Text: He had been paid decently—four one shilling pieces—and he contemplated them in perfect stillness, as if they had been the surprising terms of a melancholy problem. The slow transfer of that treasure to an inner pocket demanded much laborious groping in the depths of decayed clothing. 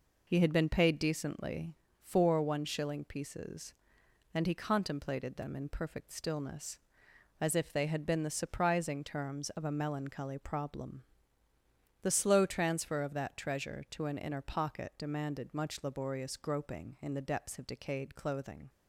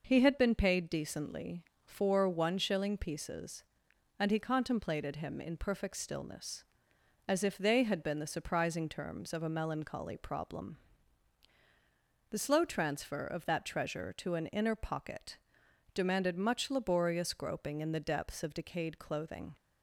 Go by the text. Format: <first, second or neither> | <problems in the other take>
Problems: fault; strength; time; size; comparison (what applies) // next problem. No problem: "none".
first | says "him" for "them"; at 5.1 s // pauses between "pocket" and "demanded"; noticeable; at 15.3 s; 0.56 s long